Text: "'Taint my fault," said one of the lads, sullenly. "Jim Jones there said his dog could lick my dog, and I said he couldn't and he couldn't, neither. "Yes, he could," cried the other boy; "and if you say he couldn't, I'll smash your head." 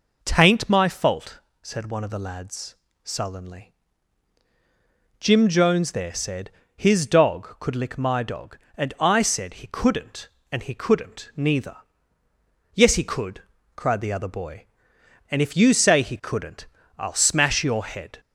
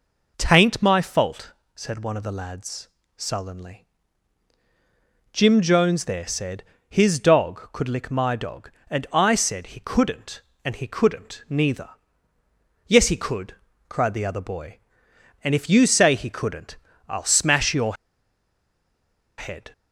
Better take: first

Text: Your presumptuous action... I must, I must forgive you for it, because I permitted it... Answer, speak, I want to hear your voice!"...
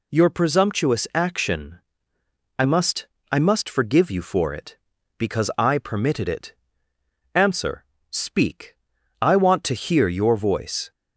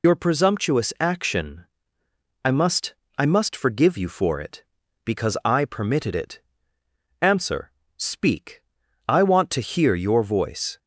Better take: first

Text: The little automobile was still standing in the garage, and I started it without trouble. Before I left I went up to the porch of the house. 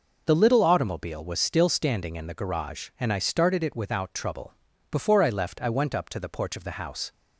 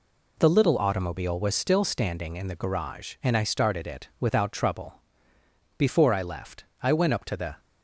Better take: first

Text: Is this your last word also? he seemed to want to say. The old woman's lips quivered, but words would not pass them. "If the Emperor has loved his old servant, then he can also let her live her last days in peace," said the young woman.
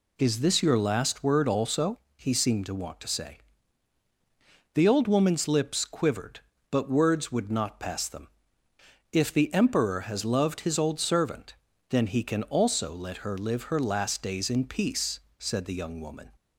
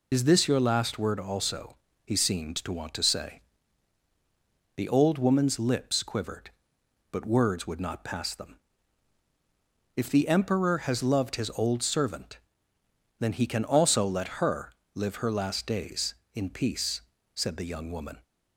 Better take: first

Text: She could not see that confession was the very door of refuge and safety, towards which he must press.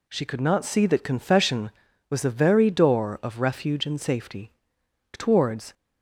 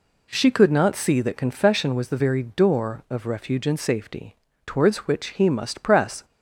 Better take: second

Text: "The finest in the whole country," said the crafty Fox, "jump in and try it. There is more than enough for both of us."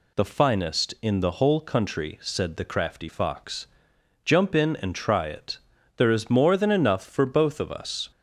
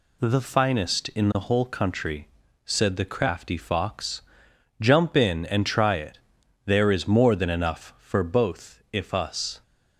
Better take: first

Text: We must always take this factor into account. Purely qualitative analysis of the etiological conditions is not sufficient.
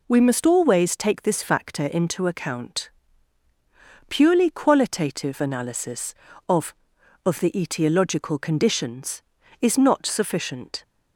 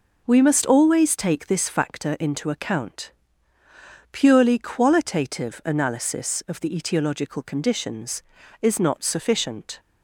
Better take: second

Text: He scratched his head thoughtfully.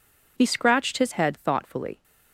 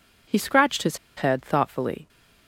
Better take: first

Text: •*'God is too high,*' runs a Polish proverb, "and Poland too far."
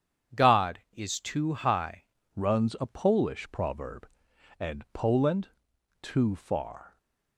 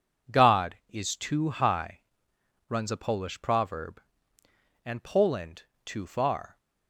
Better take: second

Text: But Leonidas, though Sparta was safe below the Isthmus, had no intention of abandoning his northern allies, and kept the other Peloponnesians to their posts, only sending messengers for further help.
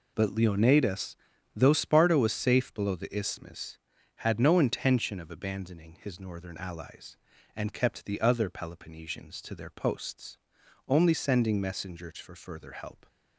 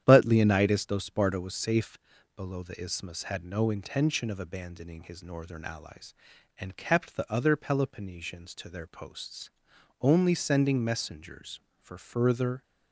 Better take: first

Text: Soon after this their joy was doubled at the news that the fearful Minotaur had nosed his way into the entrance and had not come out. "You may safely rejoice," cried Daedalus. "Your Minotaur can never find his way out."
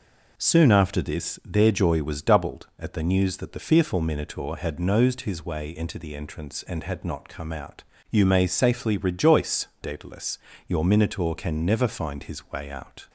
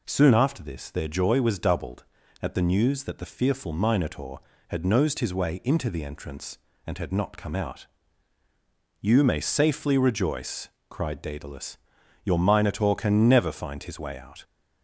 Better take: second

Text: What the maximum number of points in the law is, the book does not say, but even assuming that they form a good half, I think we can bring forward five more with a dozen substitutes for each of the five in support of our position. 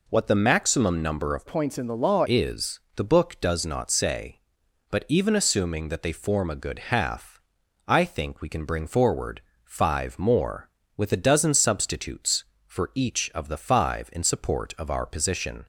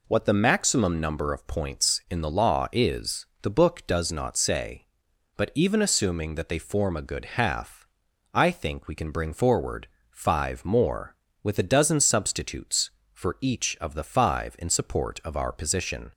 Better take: second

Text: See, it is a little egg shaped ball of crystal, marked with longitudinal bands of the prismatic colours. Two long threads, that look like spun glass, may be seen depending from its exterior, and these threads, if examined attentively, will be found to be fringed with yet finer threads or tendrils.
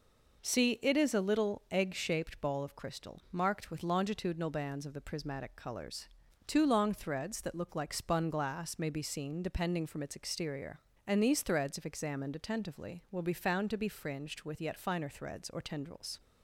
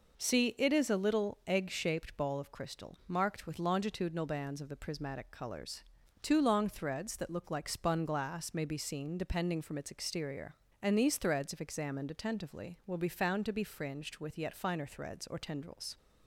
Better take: neither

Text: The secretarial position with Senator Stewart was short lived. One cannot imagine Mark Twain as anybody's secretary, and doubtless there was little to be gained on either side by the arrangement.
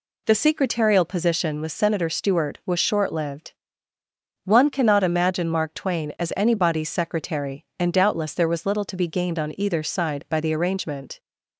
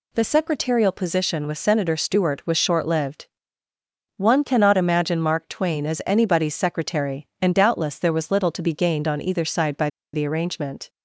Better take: first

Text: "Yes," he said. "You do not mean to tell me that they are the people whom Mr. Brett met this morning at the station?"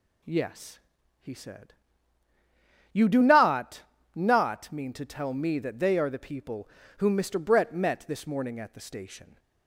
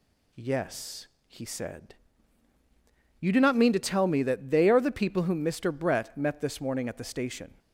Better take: second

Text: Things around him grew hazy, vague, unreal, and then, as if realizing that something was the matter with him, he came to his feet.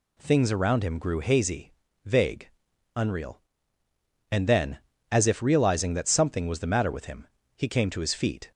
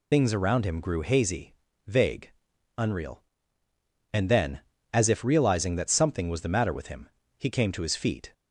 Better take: first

